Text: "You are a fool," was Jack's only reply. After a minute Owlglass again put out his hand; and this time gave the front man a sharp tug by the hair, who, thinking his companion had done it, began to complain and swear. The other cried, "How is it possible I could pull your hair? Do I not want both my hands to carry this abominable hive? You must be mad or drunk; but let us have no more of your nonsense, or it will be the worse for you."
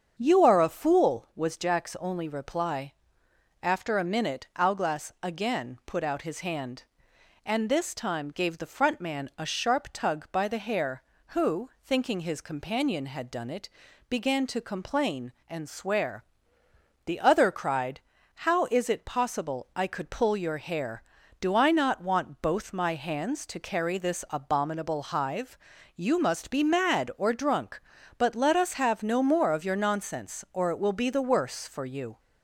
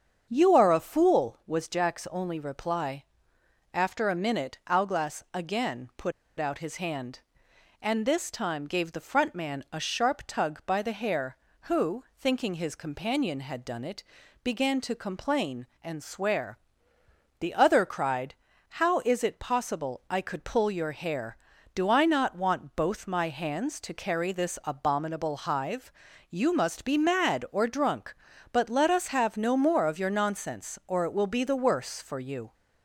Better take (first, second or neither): first